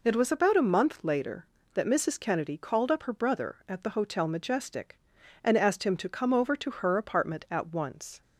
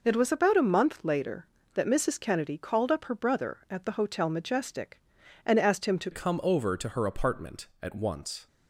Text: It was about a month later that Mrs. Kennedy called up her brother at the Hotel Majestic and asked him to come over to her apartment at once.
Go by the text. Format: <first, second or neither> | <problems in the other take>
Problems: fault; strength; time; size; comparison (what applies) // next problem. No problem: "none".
first | changes voice at "come"; from 6.1 s on; 2.3 s long